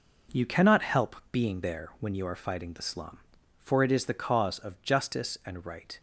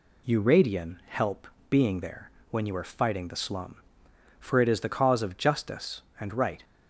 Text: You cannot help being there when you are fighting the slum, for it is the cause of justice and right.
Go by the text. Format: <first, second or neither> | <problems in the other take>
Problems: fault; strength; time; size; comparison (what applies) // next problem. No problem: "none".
first | says "radian" for "cannot"; at 0.4 s // pauses between "help" and "being"; slight; at 1.4 s; 0.22 s long; slight in the first // pauses between "there" and "when"; slight; at 2.2 s; 0.20 s long